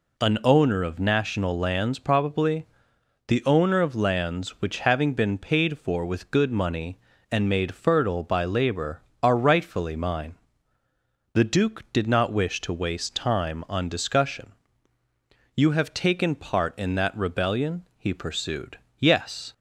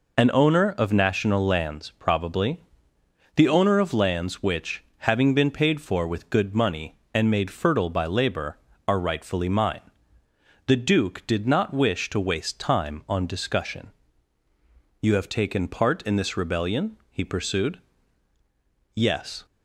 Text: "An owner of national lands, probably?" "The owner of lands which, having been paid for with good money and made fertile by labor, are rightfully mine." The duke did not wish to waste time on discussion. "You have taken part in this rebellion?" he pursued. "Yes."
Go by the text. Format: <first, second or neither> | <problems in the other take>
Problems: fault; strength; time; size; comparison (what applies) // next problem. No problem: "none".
second | says "that" for "this"; at 16.9 s